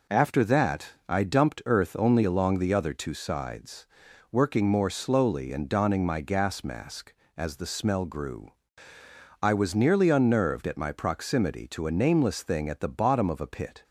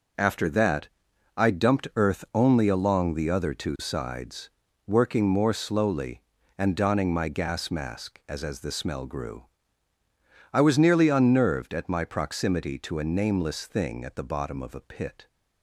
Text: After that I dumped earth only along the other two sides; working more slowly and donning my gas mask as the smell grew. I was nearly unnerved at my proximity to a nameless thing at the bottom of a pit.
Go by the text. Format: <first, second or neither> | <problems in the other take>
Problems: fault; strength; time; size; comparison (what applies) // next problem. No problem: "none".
first | pauses between "that" and "I"; noticeable; at 0.8 s; 0.48 s long; slight in the first // says "as" twice; at 8.4 s